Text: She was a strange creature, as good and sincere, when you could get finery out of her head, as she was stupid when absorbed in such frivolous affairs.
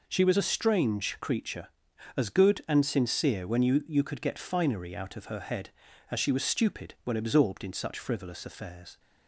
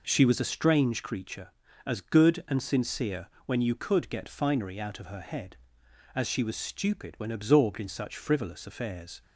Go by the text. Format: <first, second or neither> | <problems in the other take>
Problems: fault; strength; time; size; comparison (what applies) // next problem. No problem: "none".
second | says "you" twice; at 3.8 s